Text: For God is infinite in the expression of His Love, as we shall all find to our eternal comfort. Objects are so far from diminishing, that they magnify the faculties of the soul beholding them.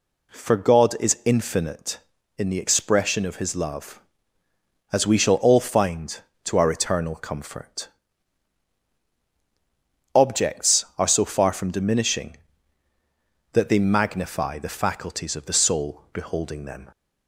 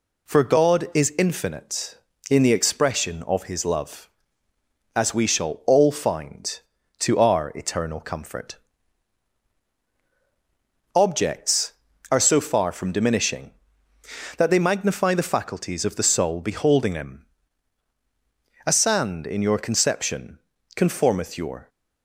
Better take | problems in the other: first | goes on to say "A sand in your conception conformeth your"; strong; from 18.6 s on; 3.0 s long

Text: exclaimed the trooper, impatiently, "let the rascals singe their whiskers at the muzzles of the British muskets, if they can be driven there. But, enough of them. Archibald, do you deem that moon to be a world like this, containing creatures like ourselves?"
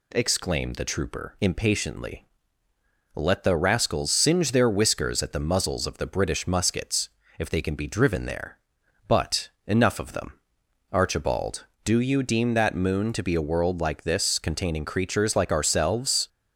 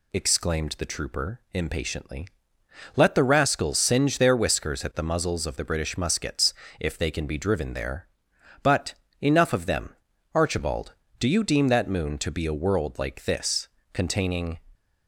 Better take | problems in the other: first | stops before "creatures like ourselves"; at 14.7 s

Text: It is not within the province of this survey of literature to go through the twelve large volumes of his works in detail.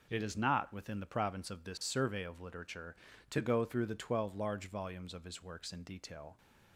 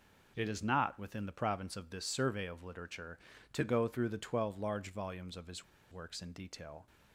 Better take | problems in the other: first | pauses between "his" and "works"; slight; at 5.6 s; 0.27 s long

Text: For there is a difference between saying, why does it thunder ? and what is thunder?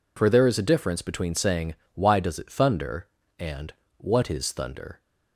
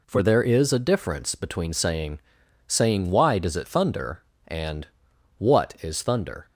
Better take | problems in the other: first | says "saying" twice; at 2.6 s // pauses between "and" and "what"; noticeable; at 4.8 s; 0.54 s long; slight in the first

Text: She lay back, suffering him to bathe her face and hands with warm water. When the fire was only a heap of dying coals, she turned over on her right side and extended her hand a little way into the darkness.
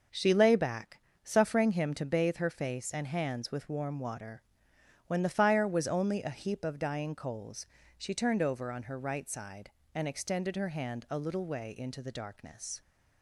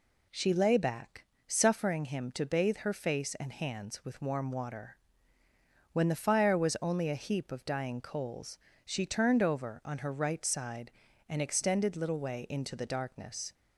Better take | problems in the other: first | skips "her hand a"; at 11.9 s

